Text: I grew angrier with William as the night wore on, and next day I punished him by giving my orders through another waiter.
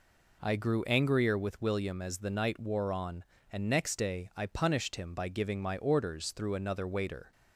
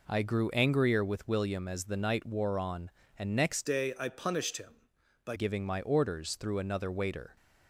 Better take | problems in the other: first | changes voice from "day" to "by"; from 3.6 to 5.3 s; 1.7 s long

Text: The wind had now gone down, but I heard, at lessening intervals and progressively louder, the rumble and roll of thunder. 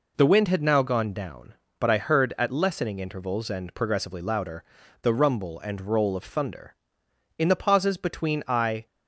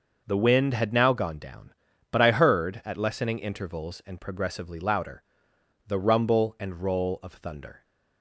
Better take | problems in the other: second | goes on to say "In the pauses between I"; from 7.3 s on; 1.4 s long

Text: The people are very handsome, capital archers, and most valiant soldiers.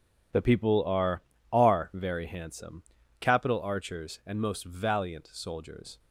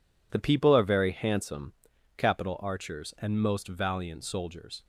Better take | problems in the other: second | says "are" twice; at 1.5 s

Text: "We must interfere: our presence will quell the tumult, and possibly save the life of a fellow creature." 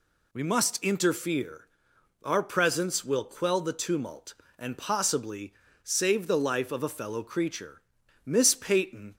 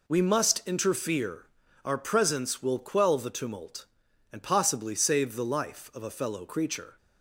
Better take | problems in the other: second | pauses between "possibly" and "save"; slight; at 5.5 s; 0.30 s long // goes on to say "Miss Peyton"; noticeable; from 8.2 s on; 0.90 s long

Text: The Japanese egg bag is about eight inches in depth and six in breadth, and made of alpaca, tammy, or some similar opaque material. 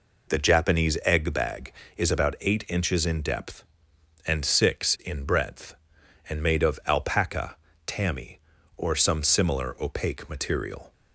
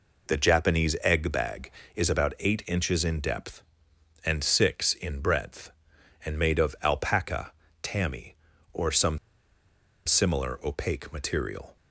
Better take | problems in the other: first | pauses between "some" and "similar"; noticeable; at 9.1 s; 0.89 s long

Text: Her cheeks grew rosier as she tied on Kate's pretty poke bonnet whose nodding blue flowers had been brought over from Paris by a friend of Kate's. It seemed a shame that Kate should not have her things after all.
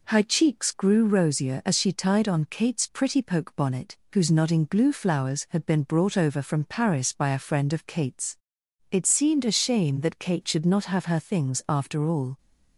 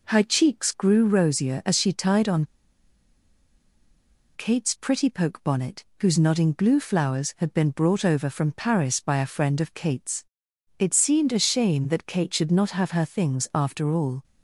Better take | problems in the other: first | pauses between "on" and "Kate's"; strong; at 2.4 s; 1.9 s long // pauses between "bonnet" and "whose"; slight; at 5.8 s; 0.16 s long; slight in the first

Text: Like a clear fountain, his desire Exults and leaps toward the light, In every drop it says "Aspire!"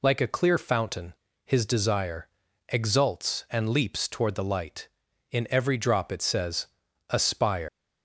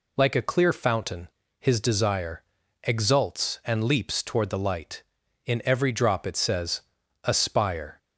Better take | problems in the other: second | pauses between "desire" and "Exults"; at 2.2 s; 0.42 s long; also in the second // pauses between "says" and "Aspire"; at 6.6 s; 0.42 s long; also in the second // leaves "Aspire" unfinished; at 7.6 s; 145 ms

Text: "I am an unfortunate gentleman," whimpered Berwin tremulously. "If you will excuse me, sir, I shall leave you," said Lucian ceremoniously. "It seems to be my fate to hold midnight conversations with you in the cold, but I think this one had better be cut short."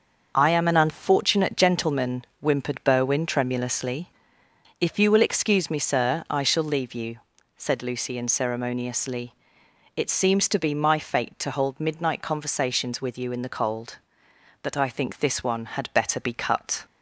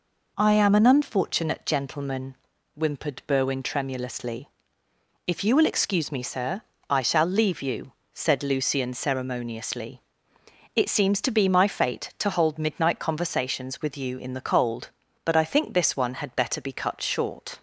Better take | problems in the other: second | starts louder than the rest; until 1.3 s; 6 dB // stops before "short"; at 16.8 s

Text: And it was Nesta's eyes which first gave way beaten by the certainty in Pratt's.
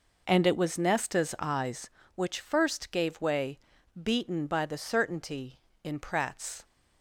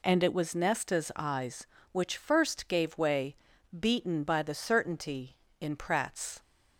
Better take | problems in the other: second | starts louder than the rest; noticeable; until 2.0 s; 5 dB // pauses between "way" and "beaten"; at 3.5 s; 0.44 s long; also in the second

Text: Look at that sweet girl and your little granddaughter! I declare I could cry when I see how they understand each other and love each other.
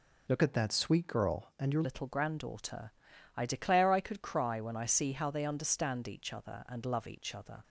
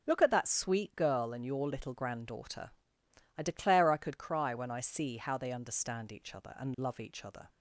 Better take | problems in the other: second | changes voice from "at" to "your"; from 0.4 to 1.8 s; 1.4 s long

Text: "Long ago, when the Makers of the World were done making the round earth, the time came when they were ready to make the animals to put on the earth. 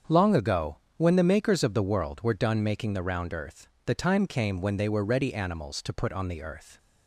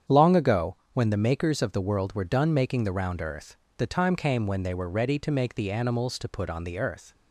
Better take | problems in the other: second | starts louder than the rest; strong; until 1.2 s; 7.5 dB; strong in the second // skips "to make the"; at 5.3 s

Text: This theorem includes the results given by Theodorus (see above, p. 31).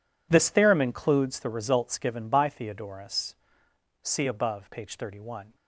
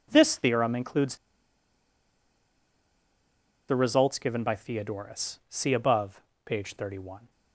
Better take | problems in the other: first | pauses between "includes" and "the"; strong; at 1.1 s; 2.5 s long

